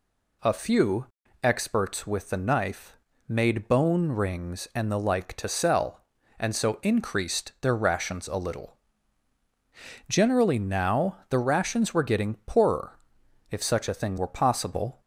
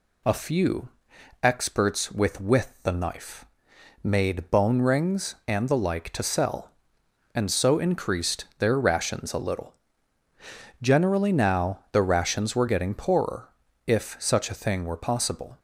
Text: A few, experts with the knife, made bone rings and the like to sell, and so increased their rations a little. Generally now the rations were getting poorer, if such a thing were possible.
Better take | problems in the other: first | says "with" twice; at 2.4 s

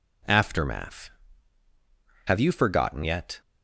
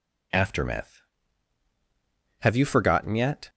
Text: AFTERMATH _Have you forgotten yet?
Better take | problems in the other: neither | none

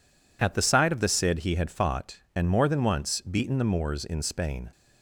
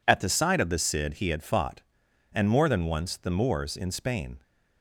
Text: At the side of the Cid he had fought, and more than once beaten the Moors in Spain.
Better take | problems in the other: first | skips "beaten"; at 3.1 s

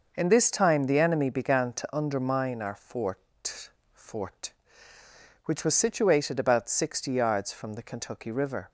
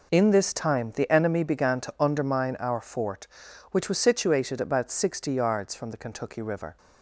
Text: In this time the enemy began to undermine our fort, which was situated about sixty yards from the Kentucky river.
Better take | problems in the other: second | says "fort" twice; at 3.9 s

